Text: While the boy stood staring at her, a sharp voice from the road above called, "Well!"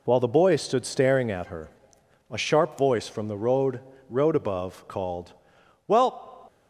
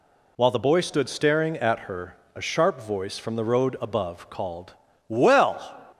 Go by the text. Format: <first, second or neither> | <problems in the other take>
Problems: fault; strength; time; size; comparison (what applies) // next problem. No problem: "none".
second | says "road" twice; at 4.0 s